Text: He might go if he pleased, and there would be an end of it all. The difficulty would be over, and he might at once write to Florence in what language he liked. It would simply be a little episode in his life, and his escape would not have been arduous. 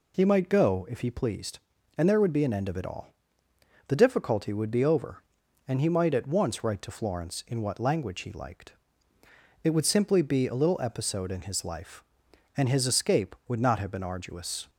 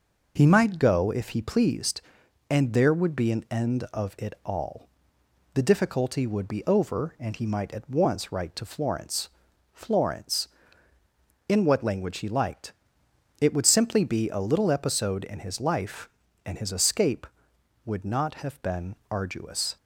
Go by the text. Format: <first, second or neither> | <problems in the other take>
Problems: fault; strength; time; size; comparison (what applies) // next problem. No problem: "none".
first | says "Florence" twice; at 9.7 s // pauses between "been" and "arduous"; slight; at 18.9 s; 0.16 s long